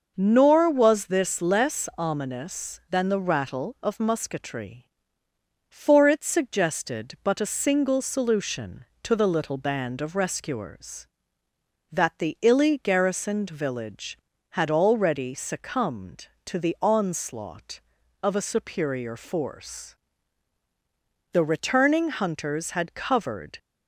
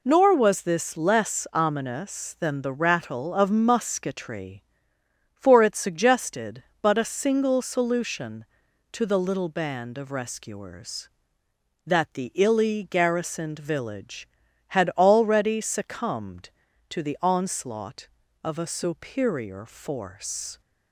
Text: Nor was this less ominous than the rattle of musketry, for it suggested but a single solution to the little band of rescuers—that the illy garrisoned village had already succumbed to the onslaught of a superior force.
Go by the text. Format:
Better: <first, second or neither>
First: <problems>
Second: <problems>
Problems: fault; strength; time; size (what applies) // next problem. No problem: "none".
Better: second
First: goes on to say "The returning hunters had covered"; strong; from 21.3 s on; 2.2 s long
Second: none